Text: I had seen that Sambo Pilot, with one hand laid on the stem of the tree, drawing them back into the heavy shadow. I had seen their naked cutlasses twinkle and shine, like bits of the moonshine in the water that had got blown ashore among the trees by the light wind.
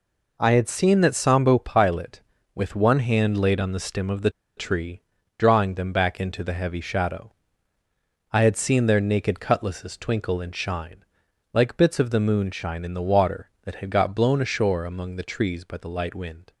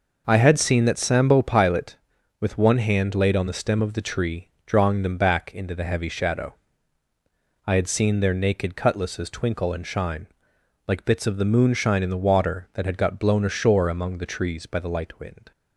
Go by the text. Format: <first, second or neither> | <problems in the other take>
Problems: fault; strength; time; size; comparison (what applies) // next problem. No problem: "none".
second | pauses between "the" and "tree"; slight; at 4.2 s; 0.27 s long